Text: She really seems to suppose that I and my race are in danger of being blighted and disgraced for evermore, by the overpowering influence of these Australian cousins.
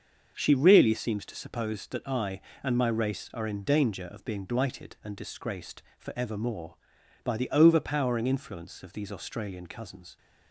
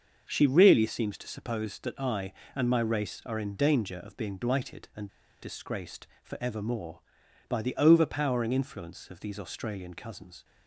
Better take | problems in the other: first | starts louder than the rest; until 1.3 s; 6.5 dB; also in the first // pauses between "and" and "disgraced"; slight; at 5.0 s; 0.34 s long

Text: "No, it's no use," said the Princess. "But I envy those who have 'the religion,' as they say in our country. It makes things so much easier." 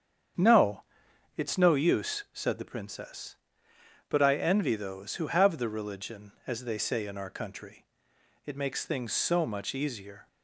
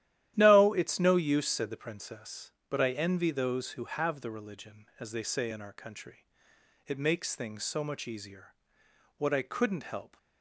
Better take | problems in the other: first | starts louder than the rest; strong; until 1.3 s; 12.5 dB; strong in the first // goes on to say "What I couldn't help"; noticeable; from 9.1 s on; 1.0 s long

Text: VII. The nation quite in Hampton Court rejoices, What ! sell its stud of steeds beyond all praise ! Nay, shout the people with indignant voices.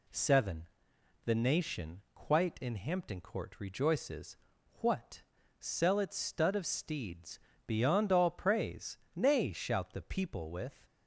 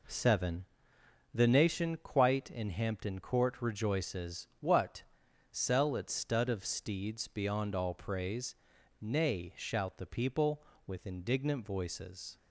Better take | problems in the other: second | pauses between "steeds" and "beyond"; slight; at 7.3 s; 0.28 s long // stops before "indignant voices"; at 10.8 s

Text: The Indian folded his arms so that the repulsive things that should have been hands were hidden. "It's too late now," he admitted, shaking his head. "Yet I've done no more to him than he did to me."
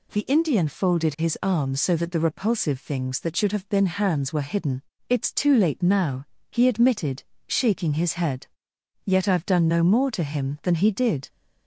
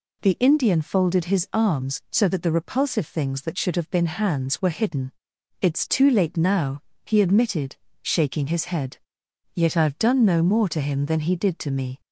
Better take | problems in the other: second | stops before "to me"; at 11.2 s

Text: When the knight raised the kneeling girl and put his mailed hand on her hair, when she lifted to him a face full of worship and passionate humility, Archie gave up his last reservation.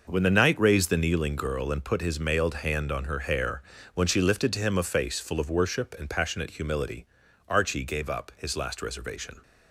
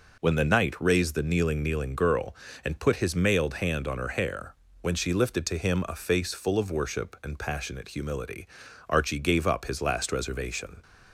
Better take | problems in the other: first | says "kneeling" twice; at 1.6 s

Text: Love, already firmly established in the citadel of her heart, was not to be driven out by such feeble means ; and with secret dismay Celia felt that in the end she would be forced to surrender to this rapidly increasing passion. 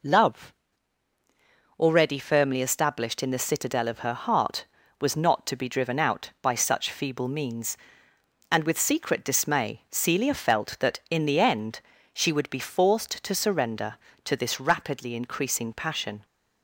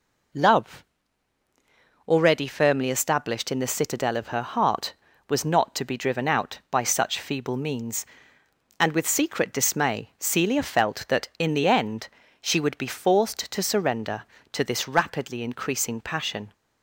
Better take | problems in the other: neither | pauses between "end" and "she"; slight; the same in both

